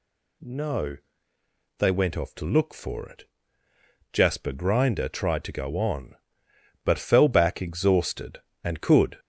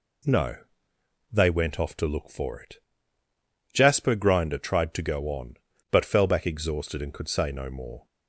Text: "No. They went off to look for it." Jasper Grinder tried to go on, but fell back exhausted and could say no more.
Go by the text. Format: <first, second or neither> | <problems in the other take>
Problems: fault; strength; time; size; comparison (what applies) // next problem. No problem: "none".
second | stops before "say no more"; at 9.1 s